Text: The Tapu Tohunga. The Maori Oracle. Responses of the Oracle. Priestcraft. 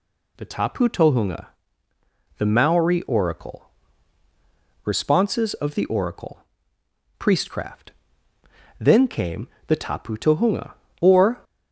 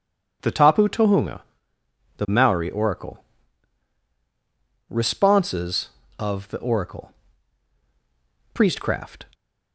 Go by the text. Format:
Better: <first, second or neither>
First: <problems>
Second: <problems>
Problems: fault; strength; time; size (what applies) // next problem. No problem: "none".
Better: second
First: goes on to say "Then came the tapu tohunga or"; strong; from 8.7 s on; 2.6 s long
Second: none